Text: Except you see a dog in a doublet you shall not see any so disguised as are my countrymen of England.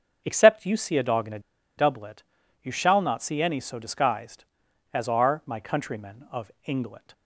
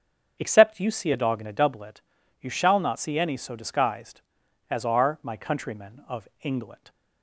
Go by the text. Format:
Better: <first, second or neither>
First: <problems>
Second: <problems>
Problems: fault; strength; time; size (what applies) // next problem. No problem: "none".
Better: second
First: starts louder than the rest; until 1.2 s; 7 dB // pauses between "a" and "doublet"; at 1.3 s; 0.38 s long // pauses between "doublet" and "you"; at 2.2 s; 0.40 s long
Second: starts louder than the rest; strong; until 1.4 s; 7.5 dB // pauses between "doublet" and "you"; at 2.0 s; 0.40 s long